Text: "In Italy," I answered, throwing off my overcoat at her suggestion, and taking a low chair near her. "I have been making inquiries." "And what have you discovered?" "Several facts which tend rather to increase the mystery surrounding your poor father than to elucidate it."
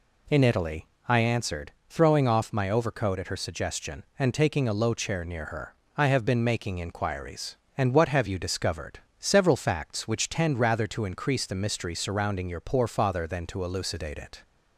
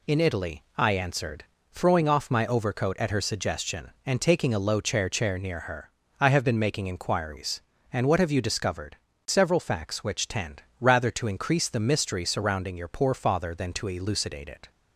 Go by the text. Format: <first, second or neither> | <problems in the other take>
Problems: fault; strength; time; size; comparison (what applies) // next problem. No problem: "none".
first | says "chair" twice; at 5.0 s // pauses between "tend" and "rather"; slight; at 10.6 s; 0.16 s long